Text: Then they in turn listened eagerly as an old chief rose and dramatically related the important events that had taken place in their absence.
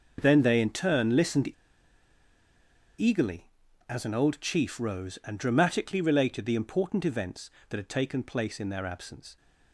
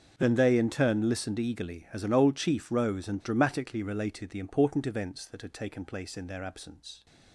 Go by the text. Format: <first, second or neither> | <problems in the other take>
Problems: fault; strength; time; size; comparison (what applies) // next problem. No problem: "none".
second | starts louder than the rest; noticeable; until 1.2 s; 6 dB; also in the second // pauses between "listened" and "eagerly"; strong; at 1.4 s; 1.4 s long